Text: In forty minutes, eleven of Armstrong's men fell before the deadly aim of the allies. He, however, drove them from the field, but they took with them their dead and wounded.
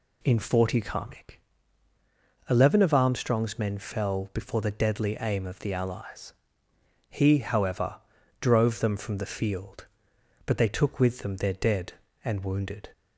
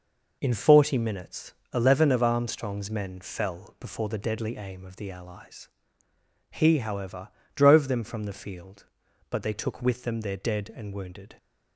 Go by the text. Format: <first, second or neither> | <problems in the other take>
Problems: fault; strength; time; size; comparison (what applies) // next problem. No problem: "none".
second | says "karmic" for "minutes"; at 0.7 s